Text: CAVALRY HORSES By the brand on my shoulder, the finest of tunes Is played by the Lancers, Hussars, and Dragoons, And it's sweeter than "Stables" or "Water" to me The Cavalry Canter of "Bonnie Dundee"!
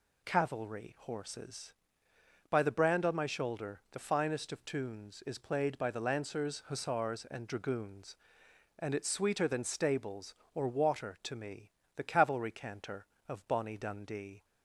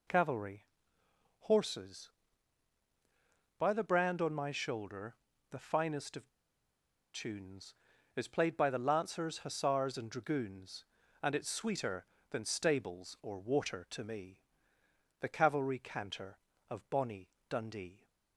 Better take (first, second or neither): first